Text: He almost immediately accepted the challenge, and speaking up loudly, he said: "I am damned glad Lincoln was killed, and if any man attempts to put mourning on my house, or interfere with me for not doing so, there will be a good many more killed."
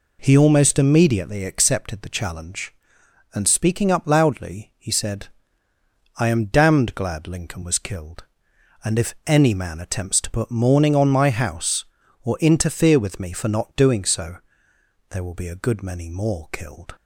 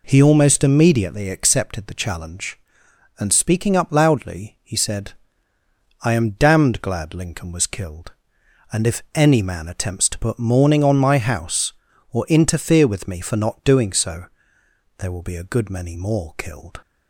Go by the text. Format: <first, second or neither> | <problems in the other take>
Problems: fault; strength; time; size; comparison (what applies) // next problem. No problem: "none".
neither | none